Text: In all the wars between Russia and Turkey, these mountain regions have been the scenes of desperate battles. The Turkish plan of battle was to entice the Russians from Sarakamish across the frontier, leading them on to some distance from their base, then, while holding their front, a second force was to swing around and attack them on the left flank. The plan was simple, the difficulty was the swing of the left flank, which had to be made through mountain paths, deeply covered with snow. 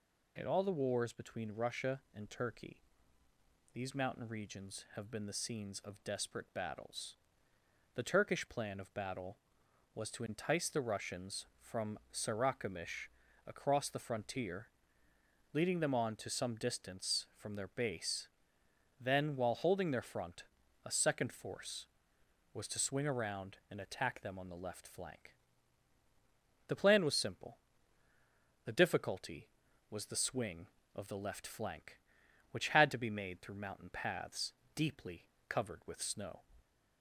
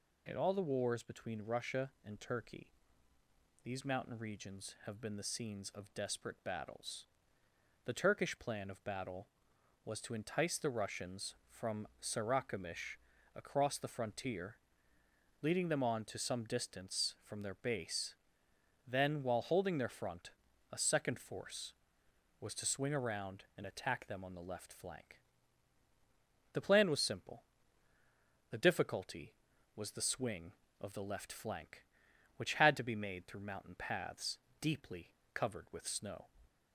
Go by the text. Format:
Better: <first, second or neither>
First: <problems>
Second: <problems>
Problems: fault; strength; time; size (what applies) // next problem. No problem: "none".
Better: neither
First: pauses between "Sarakamish" and "across"; at 13.0 s; 0.40 s long // pauses between "deeply" and "covered"; slight; at 35.2 s; 0.24 s long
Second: pauses between "Sarakamish" and "across"; at 12.9 s; 0.40 s long // pauses between "deeply" and "covered"; slight; at 35.0 s; 0.24 s long